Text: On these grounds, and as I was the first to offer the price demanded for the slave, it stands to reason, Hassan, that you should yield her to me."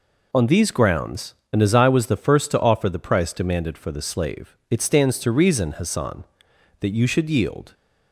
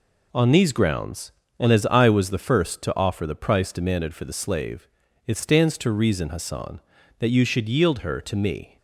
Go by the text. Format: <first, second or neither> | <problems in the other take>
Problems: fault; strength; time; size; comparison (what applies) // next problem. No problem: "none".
second | stops before "her to me"; at 7.7 s